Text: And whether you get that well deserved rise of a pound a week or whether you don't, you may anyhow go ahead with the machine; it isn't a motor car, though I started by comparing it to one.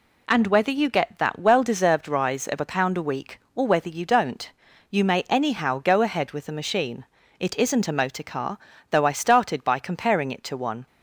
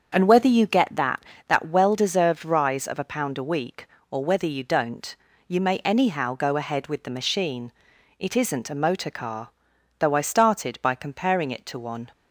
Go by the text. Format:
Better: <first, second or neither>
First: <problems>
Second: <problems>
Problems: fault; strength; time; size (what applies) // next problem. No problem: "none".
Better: first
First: none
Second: starts louder than the rest; strong; until 1.1 s; 7 dB // says "that" twice; at 1.4 s